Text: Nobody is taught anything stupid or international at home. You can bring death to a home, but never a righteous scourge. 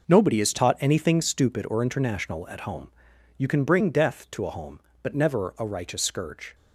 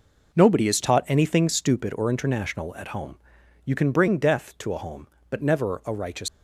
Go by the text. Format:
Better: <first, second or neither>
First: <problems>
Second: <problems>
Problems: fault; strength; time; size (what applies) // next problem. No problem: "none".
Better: first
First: none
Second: stops before "scourge"; at 6.2 s